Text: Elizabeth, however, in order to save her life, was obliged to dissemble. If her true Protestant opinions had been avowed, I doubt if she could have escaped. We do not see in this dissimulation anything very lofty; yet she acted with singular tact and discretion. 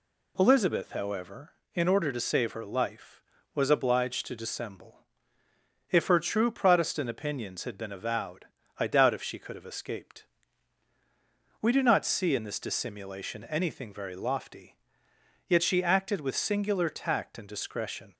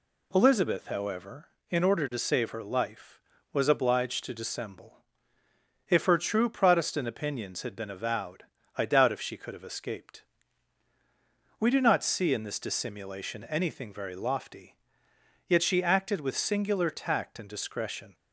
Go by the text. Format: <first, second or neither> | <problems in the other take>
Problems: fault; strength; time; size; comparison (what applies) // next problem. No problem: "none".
neither | none